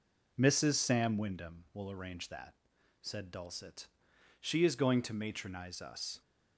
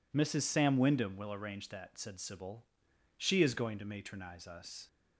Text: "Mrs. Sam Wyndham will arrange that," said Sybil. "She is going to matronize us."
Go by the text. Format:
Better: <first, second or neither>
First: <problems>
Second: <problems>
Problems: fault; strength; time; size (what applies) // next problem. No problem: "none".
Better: second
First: says "Dulcet" for "Sybil"; at 3.2 s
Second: none